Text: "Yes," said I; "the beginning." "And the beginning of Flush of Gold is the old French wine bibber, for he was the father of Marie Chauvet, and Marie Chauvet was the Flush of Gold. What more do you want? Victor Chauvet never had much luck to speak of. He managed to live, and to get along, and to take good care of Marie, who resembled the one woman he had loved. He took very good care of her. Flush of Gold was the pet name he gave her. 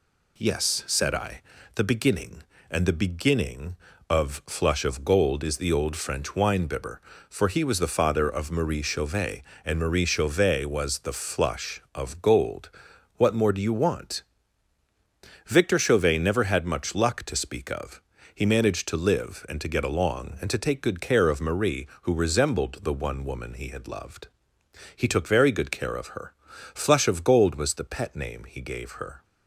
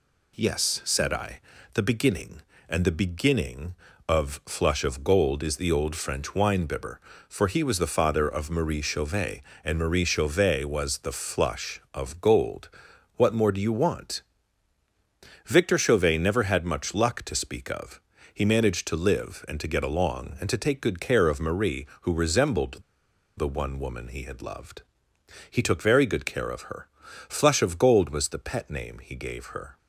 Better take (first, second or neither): first